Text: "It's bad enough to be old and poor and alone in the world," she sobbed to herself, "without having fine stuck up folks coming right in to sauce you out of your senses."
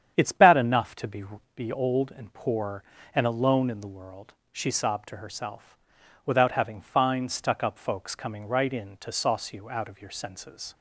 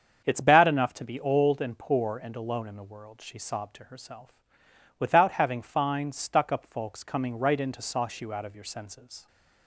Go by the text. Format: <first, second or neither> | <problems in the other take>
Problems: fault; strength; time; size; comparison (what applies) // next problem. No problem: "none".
second | starts louder than the rest; strong; until 1.1 s; 8.5 dB; strong in the second // says "be" twice; at 1.5 s